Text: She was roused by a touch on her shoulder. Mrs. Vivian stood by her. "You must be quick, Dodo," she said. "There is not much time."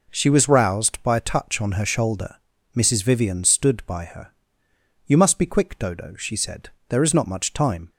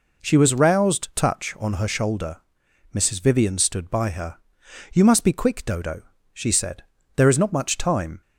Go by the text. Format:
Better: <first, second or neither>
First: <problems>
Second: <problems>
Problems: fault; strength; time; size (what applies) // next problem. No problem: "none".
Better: first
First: none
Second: skips "by a"; at 1.1 s